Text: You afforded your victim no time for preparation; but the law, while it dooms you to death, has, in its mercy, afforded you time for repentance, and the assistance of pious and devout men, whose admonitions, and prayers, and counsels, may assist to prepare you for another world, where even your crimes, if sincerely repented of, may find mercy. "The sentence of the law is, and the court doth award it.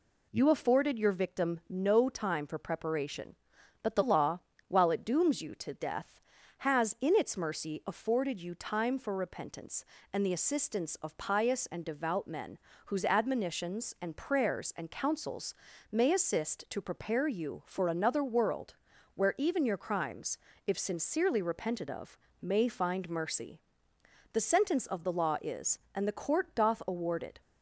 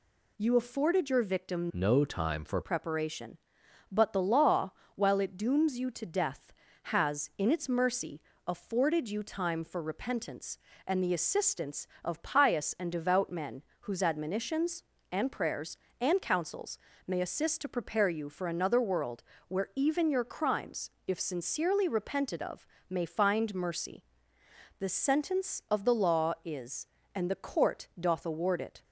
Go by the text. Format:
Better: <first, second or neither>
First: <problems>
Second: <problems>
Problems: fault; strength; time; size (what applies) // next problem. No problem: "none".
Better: first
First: none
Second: changes voice from "no" to "for"; from 1.7 to 2.6 s; 0.9 s long